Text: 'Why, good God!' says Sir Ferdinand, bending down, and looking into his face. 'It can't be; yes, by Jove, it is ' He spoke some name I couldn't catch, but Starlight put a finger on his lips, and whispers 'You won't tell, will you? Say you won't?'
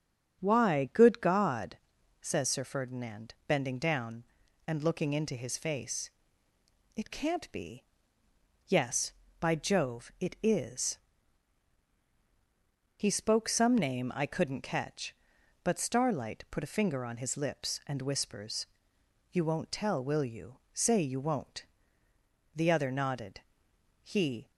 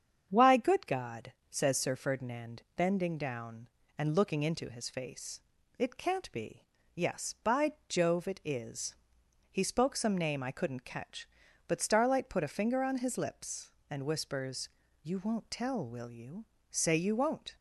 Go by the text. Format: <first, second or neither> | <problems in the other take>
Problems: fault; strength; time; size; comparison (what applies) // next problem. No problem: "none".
second | starts louder than the rest; strong; until 1.4 s; 8.5 dB; strong in the second // pauses between "whispers" and "You"; noticeable; at 18.6 s; 0.66 s long; slight in the second // goes on to say "The other nodded He"; strong; from 22.5 s on; 1.9 s long